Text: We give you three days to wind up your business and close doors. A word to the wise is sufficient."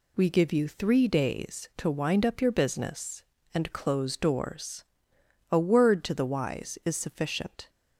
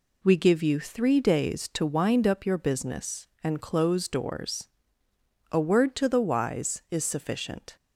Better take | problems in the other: neither | none

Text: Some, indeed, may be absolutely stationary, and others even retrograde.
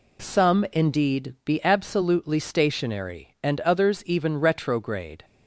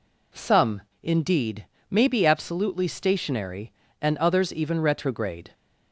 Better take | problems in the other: second | skips "may"; at 1.4 s

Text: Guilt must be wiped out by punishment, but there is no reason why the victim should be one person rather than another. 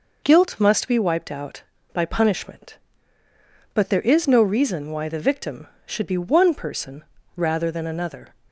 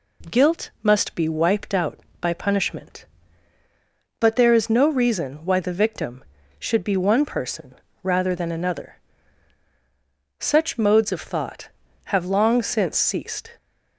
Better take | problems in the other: first | pauses between "person" and "rather"; slight; at 7.7 s; 0.30 s long; slight in the first // goes on to say "Such modes of thought have long since ceased"; strong; from 10.3 s on; 3.1 s long

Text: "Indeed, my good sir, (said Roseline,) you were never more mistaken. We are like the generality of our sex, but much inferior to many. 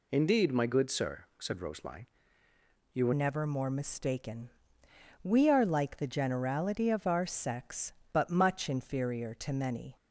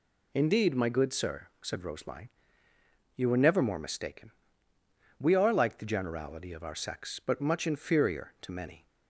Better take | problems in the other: second | changes voice at "never"; from 3.1 s on; 6.8 s long

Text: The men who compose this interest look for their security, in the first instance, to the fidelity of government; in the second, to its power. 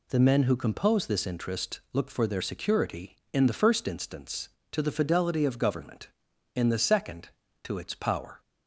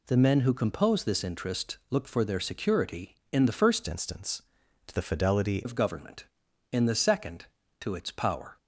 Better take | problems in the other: first | changes voice from "instance" to "fidelity"; from 3.8 to 5.6 s; 1.8 s long

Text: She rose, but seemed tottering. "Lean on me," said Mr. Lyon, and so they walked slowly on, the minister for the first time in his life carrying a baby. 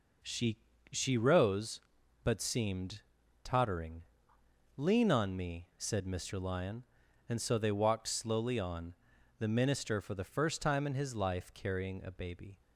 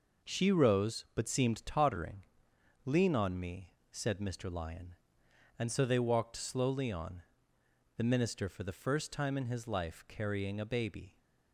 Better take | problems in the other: second | says "She" twice; at 0.9 s // pauses between "seemed" and "tottering"; at 3.0 s; 0.42 s long

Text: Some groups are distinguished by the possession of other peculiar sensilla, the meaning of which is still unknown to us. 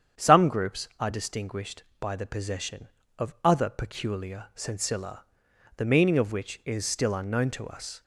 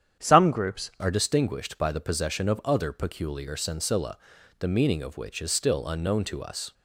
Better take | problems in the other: first | starts louder than the rest; strong; until 1.3 s; 9 dB; strong in the first // changes voice at "are"; from 0.9 s on; 5.8 s long

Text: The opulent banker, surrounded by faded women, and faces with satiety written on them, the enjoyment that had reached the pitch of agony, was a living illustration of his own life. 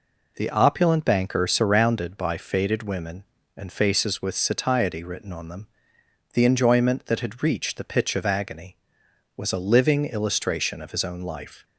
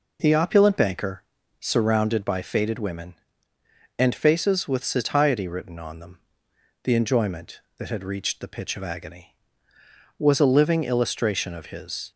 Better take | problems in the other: first | stops before "own life"; at 12.1 s

